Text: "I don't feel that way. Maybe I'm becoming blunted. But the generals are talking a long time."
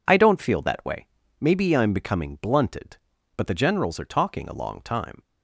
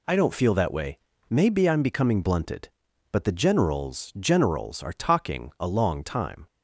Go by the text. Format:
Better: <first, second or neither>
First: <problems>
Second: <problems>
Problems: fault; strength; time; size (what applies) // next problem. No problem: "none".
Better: first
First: none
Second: says "generals" twice; at 4.1 s